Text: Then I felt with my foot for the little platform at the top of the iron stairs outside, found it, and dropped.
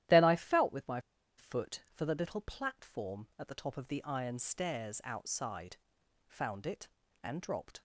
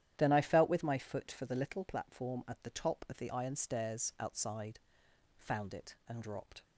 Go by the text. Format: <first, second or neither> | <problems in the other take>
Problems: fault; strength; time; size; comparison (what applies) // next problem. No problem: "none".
second | starts louder than the rest; strong; until 1.4 s; 12.5 dB; strong in the second // pauses between "my" and "foot"; at 0.9 s; 0.38 s long